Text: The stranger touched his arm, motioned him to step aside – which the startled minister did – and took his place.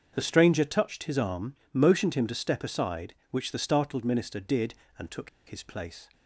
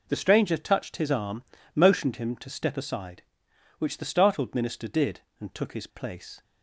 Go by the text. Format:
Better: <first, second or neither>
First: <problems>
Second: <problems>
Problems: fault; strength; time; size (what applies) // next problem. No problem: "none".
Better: second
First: starts louder than the rest; until 1.1 s; 7 dB // pauses between "took" and "his"; slight; at 5.2 s; 0.19 s long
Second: none